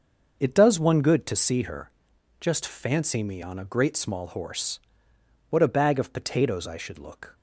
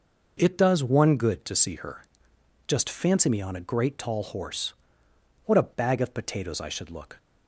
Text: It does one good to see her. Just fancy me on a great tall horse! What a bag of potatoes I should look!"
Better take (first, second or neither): second